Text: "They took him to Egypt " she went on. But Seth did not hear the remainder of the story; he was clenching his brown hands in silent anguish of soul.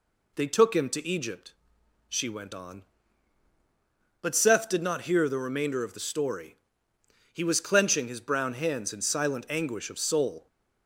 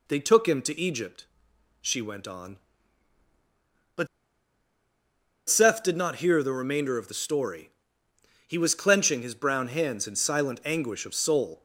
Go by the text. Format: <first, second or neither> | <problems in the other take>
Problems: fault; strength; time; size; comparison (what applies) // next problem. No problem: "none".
first | pauses between "But" and "Seth"; strong; at 4.0 s; 1.4 s long